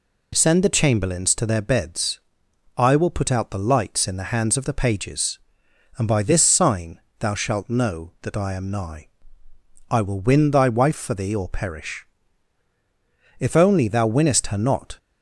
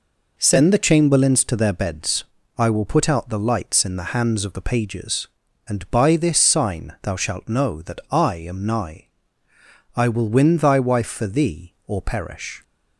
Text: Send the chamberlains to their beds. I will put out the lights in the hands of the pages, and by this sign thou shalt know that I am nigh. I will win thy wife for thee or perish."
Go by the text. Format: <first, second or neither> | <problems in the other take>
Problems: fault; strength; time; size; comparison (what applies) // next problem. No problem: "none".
second | pauses between "sign" and "thou"; slight; at 6.9 s; 0.20 s long // goes on to say "If only thou winnest her not"; from 13.3 s on; 1.6 s long